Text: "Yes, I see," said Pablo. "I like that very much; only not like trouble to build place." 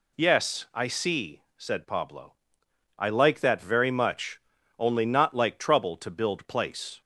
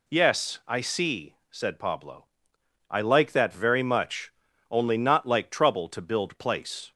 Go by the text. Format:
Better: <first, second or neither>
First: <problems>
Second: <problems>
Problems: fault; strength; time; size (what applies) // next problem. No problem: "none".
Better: neither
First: none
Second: none